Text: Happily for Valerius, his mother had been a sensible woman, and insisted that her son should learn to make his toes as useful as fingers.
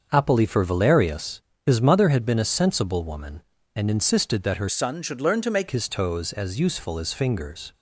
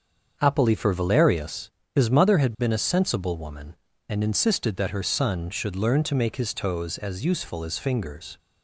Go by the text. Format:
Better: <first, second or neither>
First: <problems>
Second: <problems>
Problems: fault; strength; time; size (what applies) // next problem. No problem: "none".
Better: second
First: starts louder than the rest; until 1.1 s; 6.5 dB // changes voice from "son" to "make"; from 4.6 to 5.6 s; 1.0 s long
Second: starts louder than the rest; until 1.4 s; 7 dB